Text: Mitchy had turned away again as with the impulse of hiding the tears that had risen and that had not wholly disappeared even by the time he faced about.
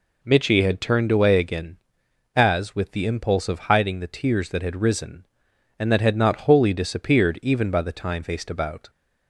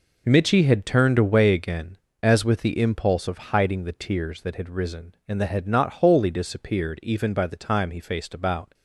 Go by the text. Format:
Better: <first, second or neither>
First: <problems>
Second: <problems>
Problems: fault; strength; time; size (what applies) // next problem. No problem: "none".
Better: second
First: skips "he"; at 8.2 s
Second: none